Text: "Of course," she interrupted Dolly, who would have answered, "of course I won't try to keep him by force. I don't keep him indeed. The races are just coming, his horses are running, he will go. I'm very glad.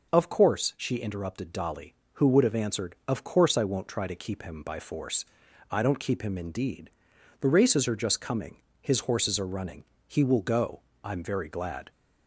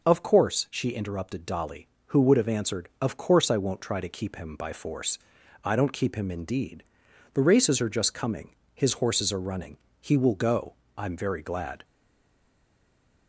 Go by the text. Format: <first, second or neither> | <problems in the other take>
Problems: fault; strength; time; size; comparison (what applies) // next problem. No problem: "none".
first | stays silent after the last word; noticeable; from 11.8 s on; 1.4 s long